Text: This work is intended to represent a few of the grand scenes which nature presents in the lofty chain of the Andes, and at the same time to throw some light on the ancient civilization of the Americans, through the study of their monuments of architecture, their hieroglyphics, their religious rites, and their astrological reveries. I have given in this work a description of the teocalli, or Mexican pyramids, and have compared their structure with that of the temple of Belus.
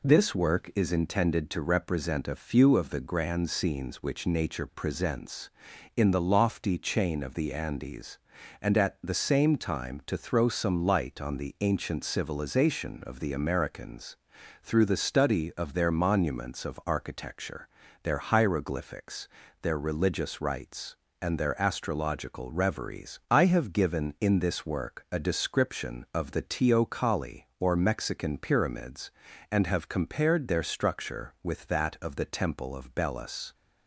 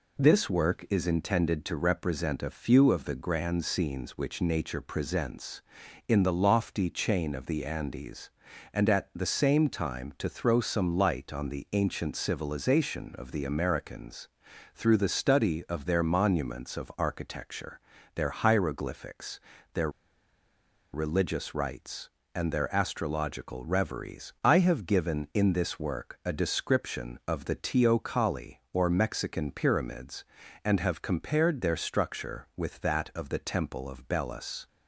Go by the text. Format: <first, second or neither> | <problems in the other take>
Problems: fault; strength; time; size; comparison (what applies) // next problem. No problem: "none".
first | pauses between "their" and "religious"; at 19.8 s; 1.0 s long